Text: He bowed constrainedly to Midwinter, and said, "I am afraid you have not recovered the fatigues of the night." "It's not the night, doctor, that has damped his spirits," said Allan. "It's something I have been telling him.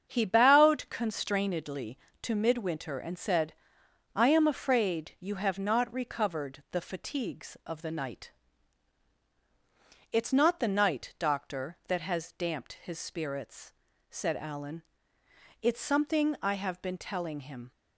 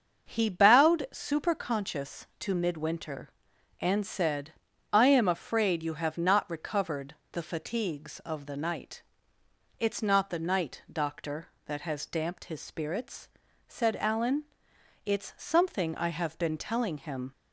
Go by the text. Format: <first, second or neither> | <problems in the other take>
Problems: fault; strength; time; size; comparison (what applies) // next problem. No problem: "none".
first | starts louder than the rest; until 1.3 s; 6.5 dB; strong in the first // says "superconscious" for "constrainedly"; at 1.1 s // pauses between "recovered" and "the"; slight; at 7.1 s; 0.16 s long